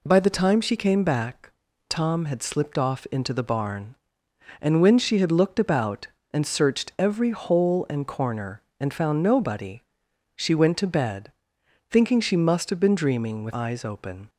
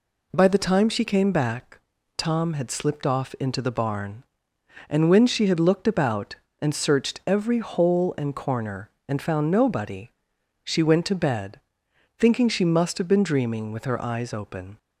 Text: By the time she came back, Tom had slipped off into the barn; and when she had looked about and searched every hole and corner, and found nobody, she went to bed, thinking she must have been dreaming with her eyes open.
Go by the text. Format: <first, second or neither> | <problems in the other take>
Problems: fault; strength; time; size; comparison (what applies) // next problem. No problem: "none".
second | skips "her"; at 13.5 s